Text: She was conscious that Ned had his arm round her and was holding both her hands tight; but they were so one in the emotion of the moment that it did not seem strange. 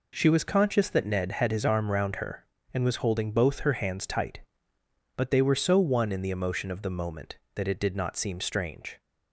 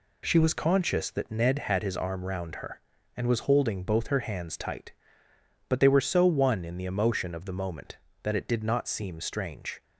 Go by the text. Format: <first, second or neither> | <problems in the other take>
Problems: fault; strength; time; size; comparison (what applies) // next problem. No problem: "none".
neither | none